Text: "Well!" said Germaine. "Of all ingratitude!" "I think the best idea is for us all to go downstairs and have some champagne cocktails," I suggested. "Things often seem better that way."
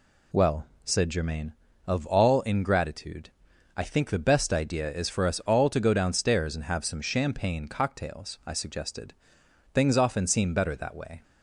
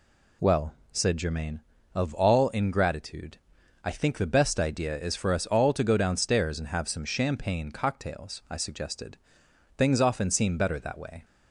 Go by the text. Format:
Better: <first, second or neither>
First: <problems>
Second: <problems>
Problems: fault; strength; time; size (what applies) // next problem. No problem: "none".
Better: neither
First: none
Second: none